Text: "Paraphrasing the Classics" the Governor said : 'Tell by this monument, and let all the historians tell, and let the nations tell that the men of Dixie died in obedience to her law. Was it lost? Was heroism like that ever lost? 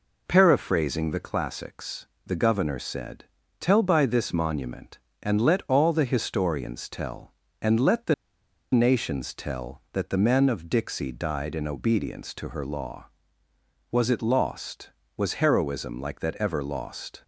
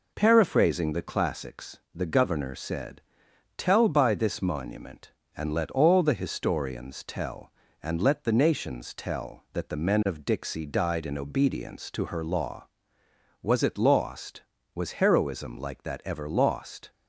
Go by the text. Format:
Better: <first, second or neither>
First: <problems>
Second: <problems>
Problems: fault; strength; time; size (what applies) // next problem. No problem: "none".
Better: second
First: pauses between "Classics" and "the"; slight; at 2.0 s; 0.20 s long // pauses between "the" and "nations"; noticeable; at 8.1 s; 0.58 s long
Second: pauses between "Classics" and "the"; slight; at 1.7 s; 0.16 s long